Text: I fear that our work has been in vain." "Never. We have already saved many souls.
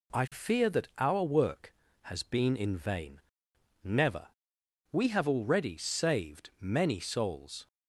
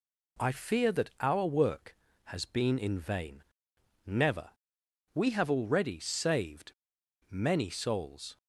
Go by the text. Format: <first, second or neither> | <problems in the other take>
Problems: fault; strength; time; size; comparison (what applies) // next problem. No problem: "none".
first | pauses between "saved" and "many"; noticeable; at 6.7 s; 0.57 s long